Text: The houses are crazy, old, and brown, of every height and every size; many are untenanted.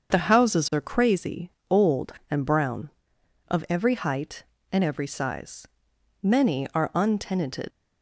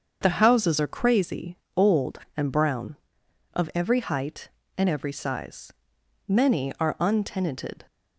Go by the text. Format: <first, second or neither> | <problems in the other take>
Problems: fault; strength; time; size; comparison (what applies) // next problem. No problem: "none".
second | starts louder than the rest; until 1.1 s; 7 dB; also in the second // leaves "untenanted" unfinished; at 7.7 s; 95 ms